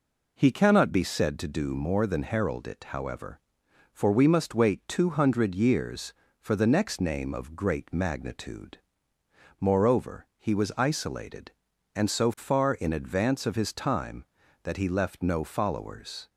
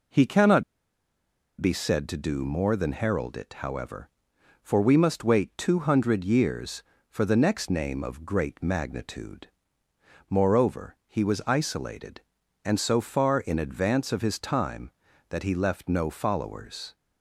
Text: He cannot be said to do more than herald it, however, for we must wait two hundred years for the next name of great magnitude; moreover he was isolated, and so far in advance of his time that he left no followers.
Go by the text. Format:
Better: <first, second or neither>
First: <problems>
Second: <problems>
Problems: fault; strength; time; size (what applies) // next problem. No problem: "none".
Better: first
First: none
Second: pauses between "cannot" and "be"; noticeable; at 0.6 s; 0.97 s long